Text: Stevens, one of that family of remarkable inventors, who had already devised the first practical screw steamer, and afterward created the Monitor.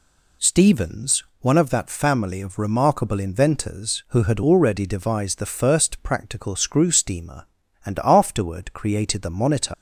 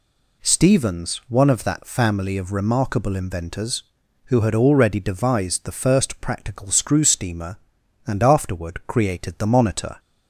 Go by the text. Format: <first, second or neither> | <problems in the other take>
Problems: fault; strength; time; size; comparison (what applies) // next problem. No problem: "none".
second | leaves "Monitor" unfinished; at 9.7 s; 150 ms